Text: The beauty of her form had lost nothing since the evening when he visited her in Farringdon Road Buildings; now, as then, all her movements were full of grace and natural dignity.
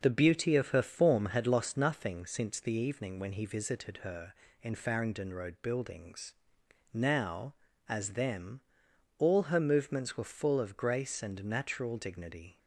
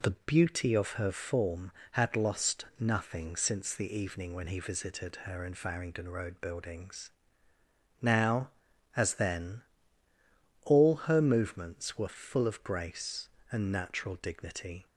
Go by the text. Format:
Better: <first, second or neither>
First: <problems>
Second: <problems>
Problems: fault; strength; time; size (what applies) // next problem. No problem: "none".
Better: second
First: says "them" for "then"; at 8.1 s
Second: none